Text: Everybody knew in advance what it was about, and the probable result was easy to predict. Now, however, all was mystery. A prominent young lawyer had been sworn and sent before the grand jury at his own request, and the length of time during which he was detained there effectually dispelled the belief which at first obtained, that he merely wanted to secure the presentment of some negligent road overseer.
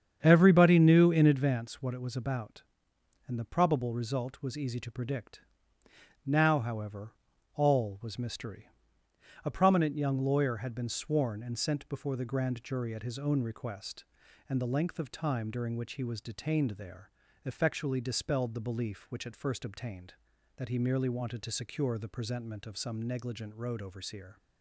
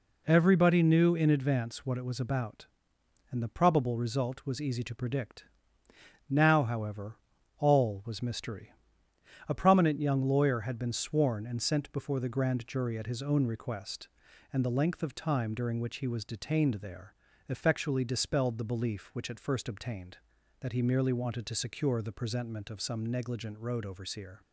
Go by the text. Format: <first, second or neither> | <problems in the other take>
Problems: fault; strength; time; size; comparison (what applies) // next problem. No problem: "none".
second | starts louder than the rest; strong; until 1.6 s; 8 dB // pauses between "there" and "effectually"; slight; at 17.0 s; 0.34 s long; slight in the second